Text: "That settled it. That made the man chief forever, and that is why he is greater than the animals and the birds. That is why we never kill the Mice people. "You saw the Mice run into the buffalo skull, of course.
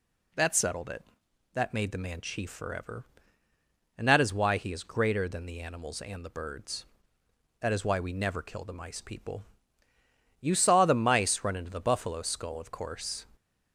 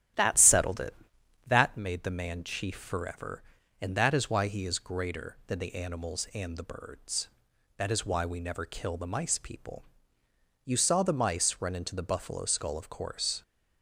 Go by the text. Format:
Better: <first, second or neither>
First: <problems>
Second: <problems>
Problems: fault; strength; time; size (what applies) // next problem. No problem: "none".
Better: first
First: none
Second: starts louder than the rest; strong; until 1.6 s; 11 dB